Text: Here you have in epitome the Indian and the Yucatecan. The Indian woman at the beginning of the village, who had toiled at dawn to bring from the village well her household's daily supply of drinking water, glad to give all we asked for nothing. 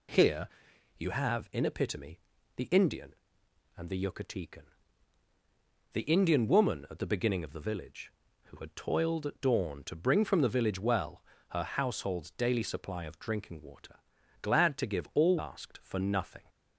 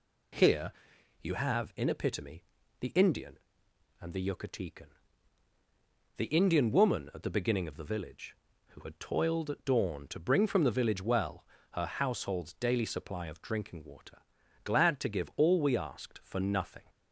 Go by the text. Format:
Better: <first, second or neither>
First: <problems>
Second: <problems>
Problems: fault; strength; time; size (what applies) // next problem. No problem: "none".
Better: second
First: pauses between "Here" and "you"; noticeable; at 0.4 s; 0.50 s long // pauses between "epitome" and "the"; at 2.1 s; 0.38 s long // pauses between "well" and "her"; slight; at 11.2 s; 0.28 s long // skips "we"; at 15.3 s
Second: pauses between "Here" and "you"; noticeable; at 0.7 s; 0.50 s long // pauses between "epitome" and "the"; at 2.4 s; 0.38 s long // pauses between "well" and "her"; slight; at 11.4 s; 0.28 s long